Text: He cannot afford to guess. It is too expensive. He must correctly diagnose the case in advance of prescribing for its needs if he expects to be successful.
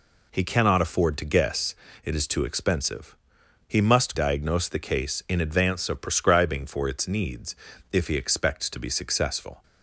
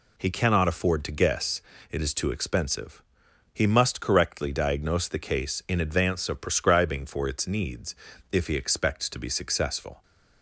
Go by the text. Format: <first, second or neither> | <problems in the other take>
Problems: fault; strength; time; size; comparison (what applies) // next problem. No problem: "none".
second | skips "correctly"; at 4.1 s // pauses between "needs" and "if"; at 7.5 s; 0.38 s long; also in the second